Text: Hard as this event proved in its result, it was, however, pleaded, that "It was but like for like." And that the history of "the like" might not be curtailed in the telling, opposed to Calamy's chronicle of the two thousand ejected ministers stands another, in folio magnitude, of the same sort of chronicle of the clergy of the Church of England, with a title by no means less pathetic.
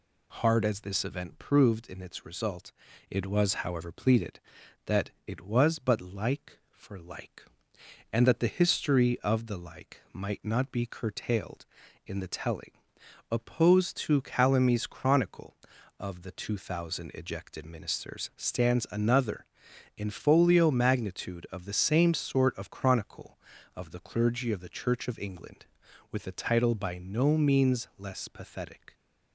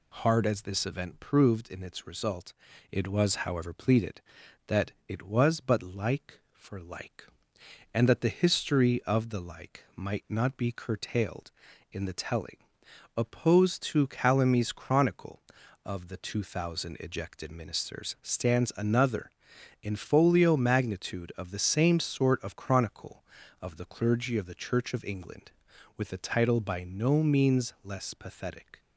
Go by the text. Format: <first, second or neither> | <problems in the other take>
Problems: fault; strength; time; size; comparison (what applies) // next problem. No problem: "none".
neither | pauses between "that" and "It"; slight; the same in both